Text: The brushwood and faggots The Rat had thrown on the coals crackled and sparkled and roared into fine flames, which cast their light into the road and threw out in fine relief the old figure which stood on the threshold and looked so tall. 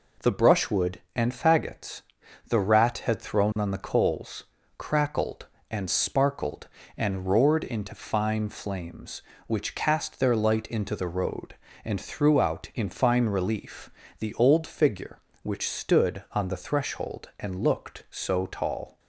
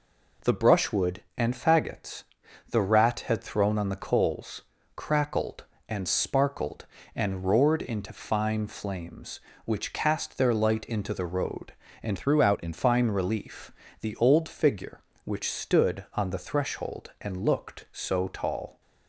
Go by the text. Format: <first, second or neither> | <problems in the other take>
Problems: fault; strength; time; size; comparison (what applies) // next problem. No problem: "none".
first | pauses between "faggots" and "The"; noticeable; at 2.2 s; 0.48 s long; noticeable in the first // pauses between "coals" and "crackled"; slight; at 4.6 s; 0.32 s long; slight in the first // changes voice from "threw" to "in"; from 12.1 to 12.7 s; 0.6 s long // pauses between "relief" and "the"; slight; at 13.7 s; 0.30 s long; slight in the first